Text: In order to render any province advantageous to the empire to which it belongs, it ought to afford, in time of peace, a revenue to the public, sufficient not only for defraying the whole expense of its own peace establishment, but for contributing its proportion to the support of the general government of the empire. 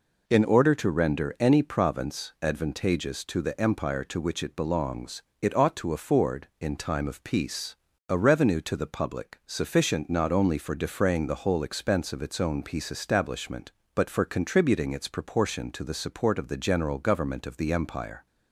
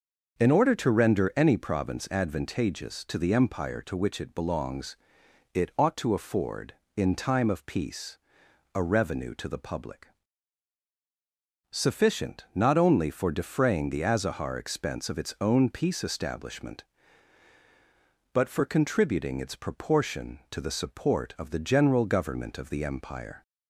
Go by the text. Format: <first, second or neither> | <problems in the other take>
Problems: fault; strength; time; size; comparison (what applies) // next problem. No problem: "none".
first | starts louder than the rest; until 1.4 s; 6.5 dB // says "azahar" for "whole"; at 14.0 s